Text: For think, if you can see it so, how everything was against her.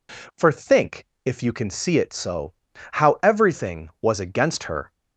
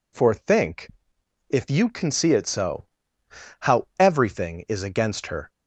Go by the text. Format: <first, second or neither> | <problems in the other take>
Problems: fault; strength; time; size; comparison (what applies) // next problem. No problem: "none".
first | says "is" for "was"; at 4.6 s